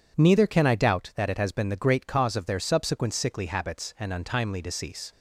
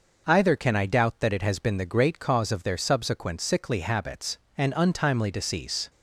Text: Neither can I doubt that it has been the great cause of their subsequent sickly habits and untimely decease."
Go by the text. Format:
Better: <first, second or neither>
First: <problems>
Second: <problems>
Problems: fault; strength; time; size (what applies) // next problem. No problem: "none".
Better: first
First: none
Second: says "Either" for "Neither"; at 0.2 s